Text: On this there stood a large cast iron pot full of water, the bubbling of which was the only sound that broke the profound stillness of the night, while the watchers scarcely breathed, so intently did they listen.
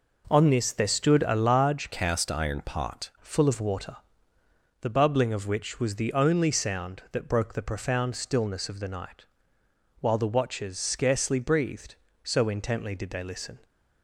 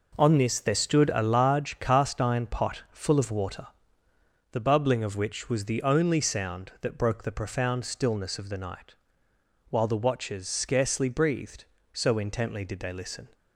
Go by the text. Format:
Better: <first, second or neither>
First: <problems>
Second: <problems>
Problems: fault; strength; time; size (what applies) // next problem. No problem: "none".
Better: second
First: changes voice from "cast" to "pot"; from 1.9 to 3.1 s; 1.2 s long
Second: none